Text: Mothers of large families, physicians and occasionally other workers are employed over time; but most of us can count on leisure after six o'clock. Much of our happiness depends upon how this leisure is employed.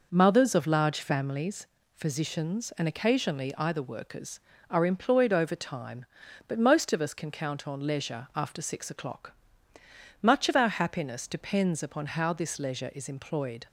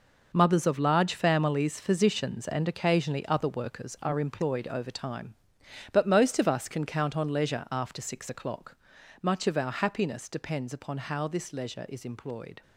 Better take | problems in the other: second | says "either" for "other"; at 3.5 s

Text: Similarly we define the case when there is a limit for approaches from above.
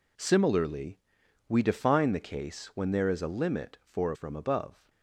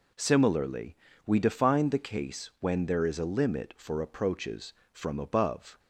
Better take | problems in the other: second | pauses between "Similarly" and "we"; noticeable; at 0.9 s; 0.52 s long; slight in the second // skips "approaches"; at 4.1 s

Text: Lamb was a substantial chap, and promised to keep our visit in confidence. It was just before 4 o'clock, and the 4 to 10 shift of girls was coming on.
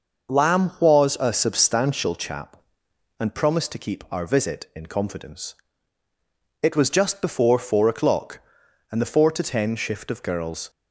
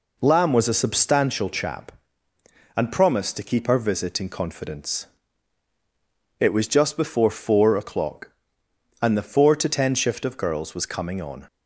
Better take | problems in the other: second | stops before "was coming on"; at 10.6 s

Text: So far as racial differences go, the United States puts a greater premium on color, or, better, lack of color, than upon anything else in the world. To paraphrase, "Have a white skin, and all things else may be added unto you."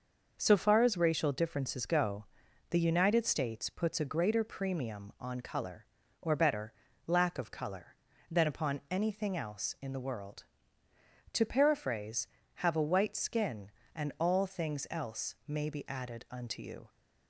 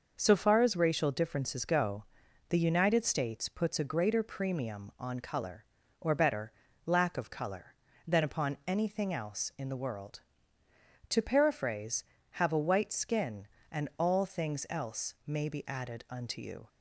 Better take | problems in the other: neither | none

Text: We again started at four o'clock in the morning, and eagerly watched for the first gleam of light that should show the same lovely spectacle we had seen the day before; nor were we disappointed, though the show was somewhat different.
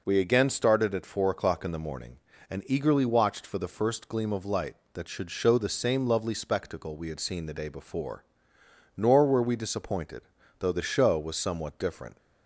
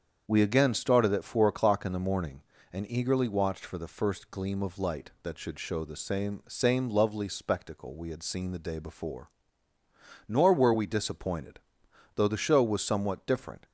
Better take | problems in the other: first | starts louder than the rest; strong; until 1.2 s; 7.5 dB // says "same" twice; at 6.4 s

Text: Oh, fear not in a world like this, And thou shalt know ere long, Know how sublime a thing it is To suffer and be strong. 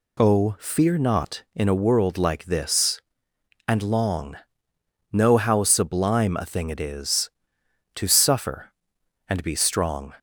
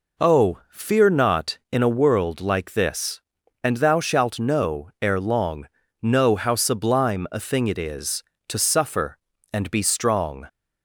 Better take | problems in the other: second | skips "thou shalt know ere"; at 3.8 s

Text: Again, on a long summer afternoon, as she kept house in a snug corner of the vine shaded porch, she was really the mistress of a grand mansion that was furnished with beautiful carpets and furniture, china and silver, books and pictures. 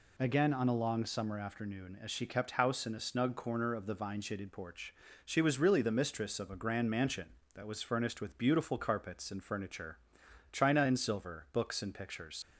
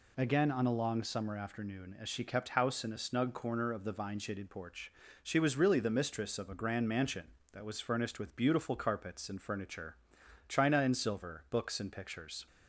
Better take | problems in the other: second | leaves "pictures" unfinished; at 12.4 s; 60 ms

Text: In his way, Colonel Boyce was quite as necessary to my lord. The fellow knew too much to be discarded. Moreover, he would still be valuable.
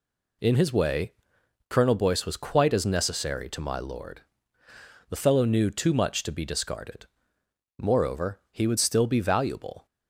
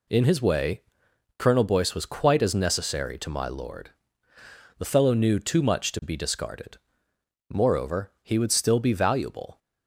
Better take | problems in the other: neither | none

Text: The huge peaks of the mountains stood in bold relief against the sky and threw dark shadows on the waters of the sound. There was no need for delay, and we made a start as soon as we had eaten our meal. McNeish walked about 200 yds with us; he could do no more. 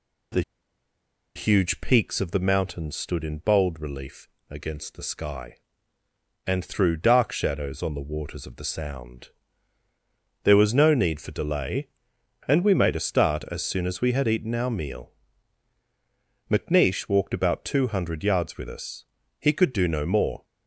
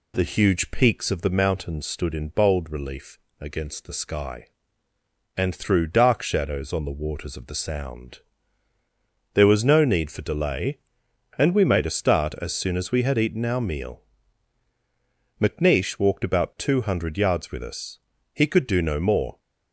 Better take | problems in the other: second | pauses between "The" and "huge"; noticeable; at 0.4 s; 0.94 s long // pauses between "relief" and "against"; slight; at 4.2 s; 0.22 s long; slight in the second

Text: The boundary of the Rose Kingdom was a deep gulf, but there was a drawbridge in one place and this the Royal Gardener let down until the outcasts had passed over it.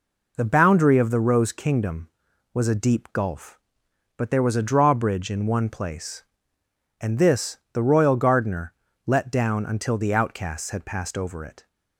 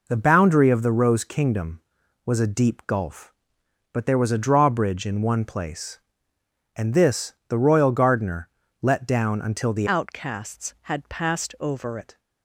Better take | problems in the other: first | pauses between "Gardener" and "let"; slight; at 8.4 s; 0.32 s long; slight in the first // changes voice from "outcasts" to "over"; from 9.8 to 11.9 s; 2.1 s long

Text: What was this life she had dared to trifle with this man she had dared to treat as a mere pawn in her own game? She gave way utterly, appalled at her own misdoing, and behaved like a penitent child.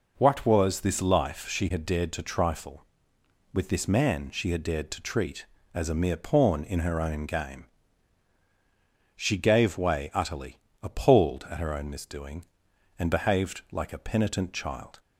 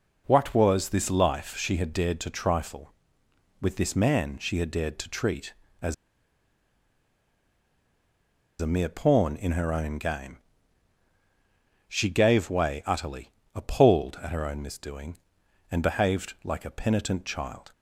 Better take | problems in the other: first | pauses between "as" and "a"; strong; at 5.9 s; 2.6 s long

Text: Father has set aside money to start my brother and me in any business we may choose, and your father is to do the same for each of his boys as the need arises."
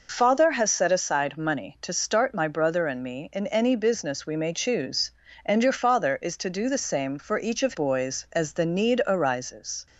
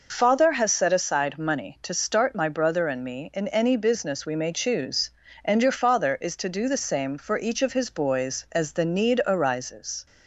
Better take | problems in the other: second | skips "his"; at 7.7 s

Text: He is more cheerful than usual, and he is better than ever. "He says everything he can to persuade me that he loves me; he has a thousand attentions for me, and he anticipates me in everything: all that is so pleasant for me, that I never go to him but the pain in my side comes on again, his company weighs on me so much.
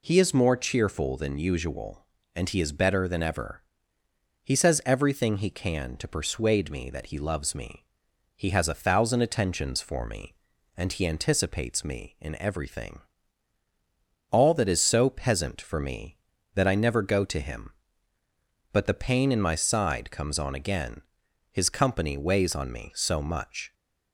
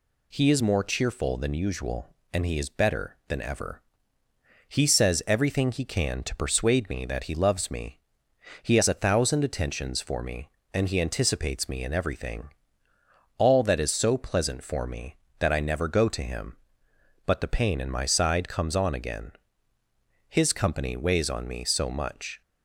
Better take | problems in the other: second | says "peasant" for "pleasant"; at 15.0 s

